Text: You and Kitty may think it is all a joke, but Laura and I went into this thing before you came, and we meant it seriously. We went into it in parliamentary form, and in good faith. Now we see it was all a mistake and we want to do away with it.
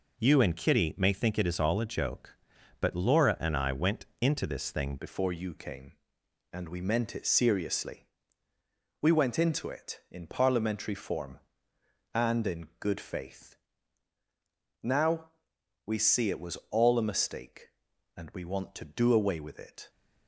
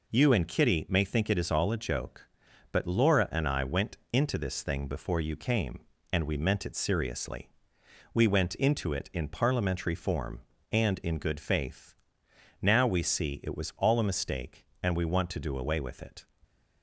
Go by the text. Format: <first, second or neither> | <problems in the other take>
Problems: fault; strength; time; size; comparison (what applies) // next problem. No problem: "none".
second | pauses between "went" and "into"; slight; at 4.0 s; 0.16 s long; slight in the second // changes voice at "before"; from 4.9 s on; 14.9 s long // pauses between "Now" and "we"; noticeable; at 15.2 s; 0.58 s long